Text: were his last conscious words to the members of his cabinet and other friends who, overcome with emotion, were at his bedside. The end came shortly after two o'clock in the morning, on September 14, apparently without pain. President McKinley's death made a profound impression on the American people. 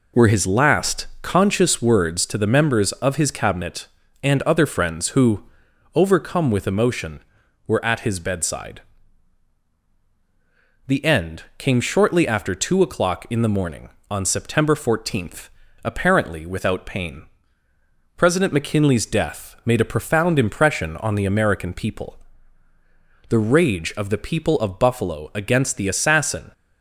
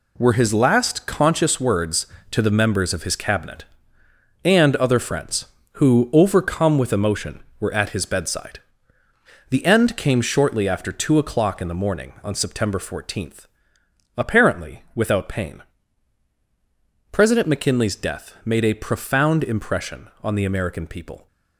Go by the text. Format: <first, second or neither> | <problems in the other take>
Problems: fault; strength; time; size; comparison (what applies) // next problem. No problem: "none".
second | pauses between "end" and "came"; slight; at 11.4 s; 0.16 s long // goes on to say "The rage of the people of Buffalo against the assassin"; strong; from 23.2 s on; 3.2 s long